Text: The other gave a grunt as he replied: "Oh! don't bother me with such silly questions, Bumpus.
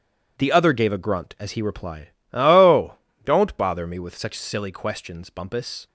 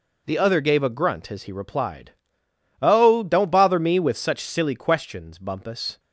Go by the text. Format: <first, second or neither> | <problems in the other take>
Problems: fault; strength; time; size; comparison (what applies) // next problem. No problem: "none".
neither | none